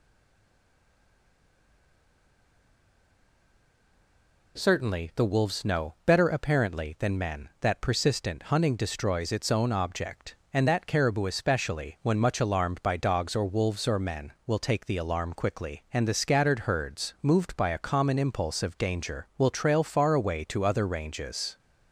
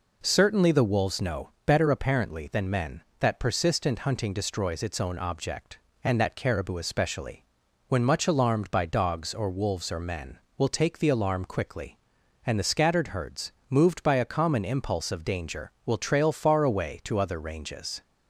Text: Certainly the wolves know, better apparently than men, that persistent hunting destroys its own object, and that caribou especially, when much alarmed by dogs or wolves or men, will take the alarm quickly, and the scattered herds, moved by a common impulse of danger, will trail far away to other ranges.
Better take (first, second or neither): second